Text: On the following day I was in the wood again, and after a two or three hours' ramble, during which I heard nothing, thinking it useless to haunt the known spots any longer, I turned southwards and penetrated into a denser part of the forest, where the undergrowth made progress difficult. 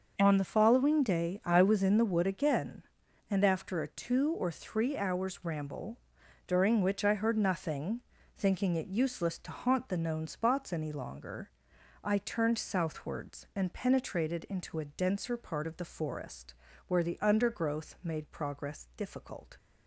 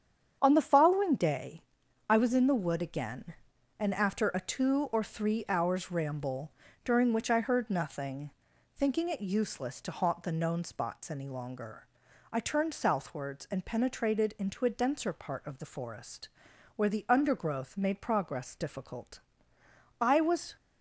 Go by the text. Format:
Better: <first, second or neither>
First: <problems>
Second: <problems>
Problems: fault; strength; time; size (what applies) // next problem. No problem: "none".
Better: first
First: starts louder than the rest; until 1.1 s; 6 dB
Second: starts louder than the rest; strong; until 1.4 s; 8 dB // pauses between "day" and "I"; at 1.6 s; 0.44 s long // goes on to say "I was"; from 20.0 s on; 0.54 s long